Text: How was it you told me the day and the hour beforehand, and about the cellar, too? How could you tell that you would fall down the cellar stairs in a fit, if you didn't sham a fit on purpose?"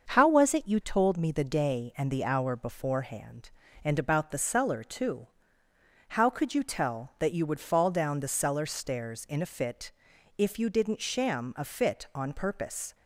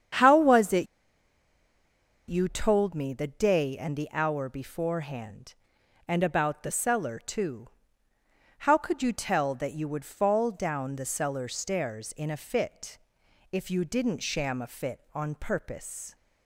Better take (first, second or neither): first